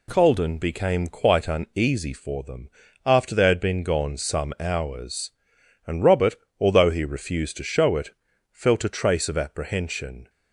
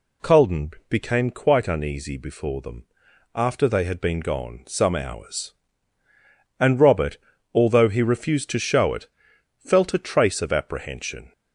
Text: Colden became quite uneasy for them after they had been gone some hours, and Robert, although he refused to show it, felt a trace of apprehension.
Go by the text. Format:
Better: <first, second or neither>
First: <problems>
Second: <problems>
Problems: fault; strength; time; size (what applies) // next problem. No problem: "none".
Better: first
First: pauses between "them" and "after"; slight; at 2.6 s; 0.36 s long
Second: pauses between "Colden" and "became"; slight; at 0.7 s; 0.18 s long // says "before" for "for"; at 2.1 s // pauses between "them" and "after"; noticeable; at 2.8 s; 0.50 s long